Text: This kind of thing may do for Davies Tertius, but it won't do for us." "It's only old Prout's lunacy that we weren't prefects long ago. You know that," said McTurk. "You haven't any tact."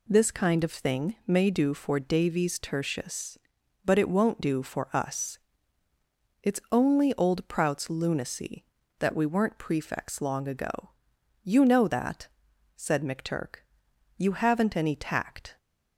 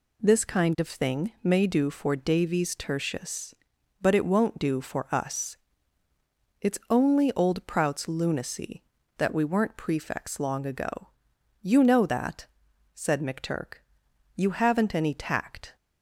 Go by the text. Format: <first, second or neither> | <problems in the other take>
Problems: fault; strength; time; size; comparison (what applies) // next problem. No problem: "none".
neither | none